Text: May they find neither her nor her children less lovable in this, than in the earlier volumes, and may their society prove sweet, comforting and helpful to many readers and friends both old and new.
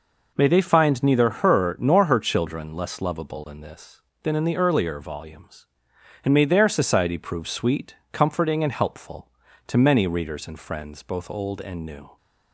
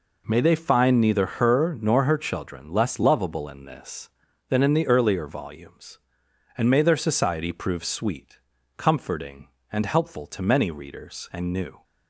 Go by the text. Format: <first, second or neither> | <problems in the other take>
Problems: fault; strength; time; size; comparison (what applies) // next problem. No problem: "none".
first | skips "friends both old and"; at 11.5 s